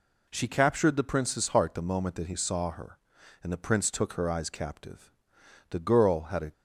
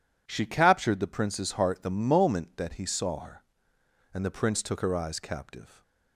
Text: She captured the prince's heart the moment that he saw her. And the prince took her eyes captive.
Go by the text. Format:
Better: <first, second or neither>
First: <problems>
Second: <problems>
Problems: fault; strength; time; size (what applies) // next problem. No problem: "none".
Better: second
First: goes on to say "The girl had a"; noticeable; from 5.7 s on; 0.82 s long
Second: none